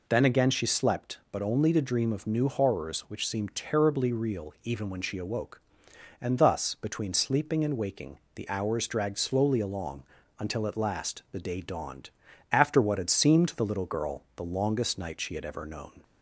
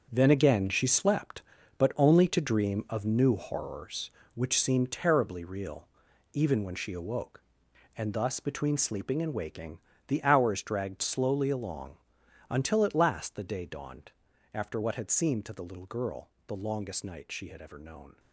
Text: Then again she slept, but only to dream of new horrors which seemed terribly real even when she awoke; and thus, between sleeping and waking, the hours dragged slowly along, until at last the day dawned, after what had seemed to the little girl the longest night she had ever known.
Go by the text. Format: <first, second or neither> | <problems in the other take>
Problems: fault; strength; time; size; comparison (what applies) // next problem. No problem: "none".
first | gets quieter; strong; throughout; 10 dB // pauses between "real" and "even"; noticeable; at 5.8 s; 0.46 s long // pauses between "girl" and "the"; slight; at 16.2 s; 0.18 s long